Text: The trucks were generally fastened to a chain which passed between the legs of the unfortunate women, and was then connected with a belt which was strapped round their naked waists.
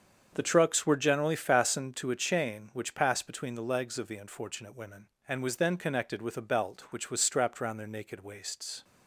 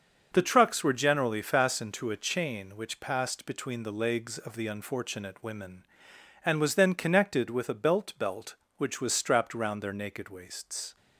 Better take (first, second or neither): first